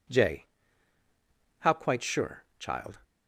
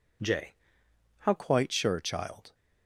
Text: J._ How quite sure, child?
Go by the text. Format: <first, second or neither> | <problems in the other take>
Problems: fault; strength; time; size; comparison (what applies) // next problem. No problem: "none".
first | changes voice at "quite"; from 1.3 s on; 1.2 s long